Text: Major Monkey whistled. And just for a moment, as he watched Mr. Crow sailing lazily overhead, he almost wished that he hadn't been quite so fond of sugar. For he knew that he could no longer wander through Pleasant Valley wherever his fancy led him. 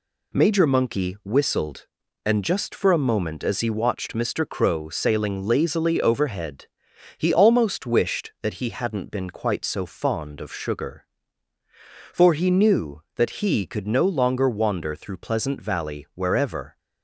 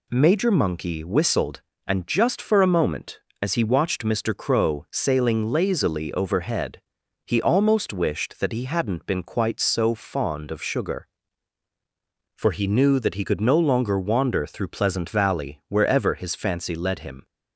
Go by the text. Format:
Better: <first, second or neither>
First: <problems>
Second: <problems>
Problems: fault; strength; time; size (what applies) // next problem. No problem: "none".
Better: second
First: stops before "his fancy led him"; at 16.7 s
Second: none